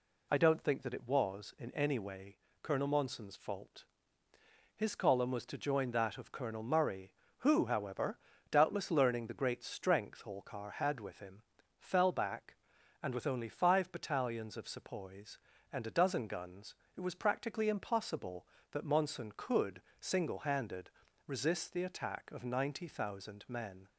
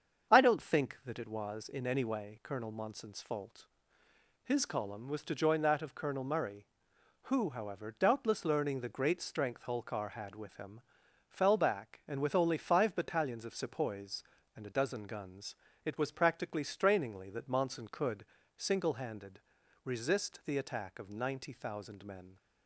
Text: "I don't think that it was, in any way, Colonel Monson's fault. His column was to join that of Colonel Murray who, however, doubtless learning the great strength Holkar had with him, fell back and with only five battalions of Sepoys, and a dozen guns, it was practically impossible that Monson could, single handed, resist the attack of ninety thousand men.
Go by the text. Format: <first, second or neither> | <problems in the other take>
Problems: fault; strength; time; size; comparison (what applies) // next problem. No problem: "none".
first | starts louder than the rest; strong; until 1.3 s; 7.5 dB // says "strainingly" for "impossible"; at 16.6 s